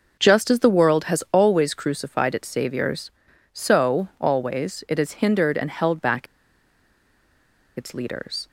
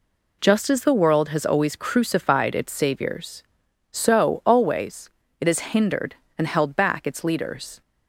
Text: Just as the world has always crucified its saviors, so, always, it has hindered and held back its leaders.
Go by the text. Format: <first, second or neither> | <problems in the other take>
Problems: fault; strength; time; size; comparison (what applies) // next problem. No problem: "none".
second | pauses between "back" and "its"; strong; at 6.2 s; 1.5 s long